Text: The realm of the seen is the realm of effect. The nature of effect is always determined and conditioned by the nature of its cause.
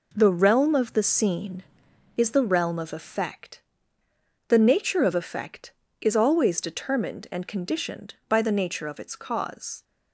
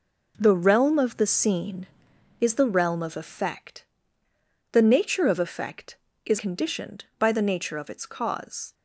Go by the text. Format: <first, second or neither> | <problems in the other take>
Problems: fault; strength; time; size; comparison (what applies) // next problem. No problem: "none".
first | skips "always determined and"; at 6.3 s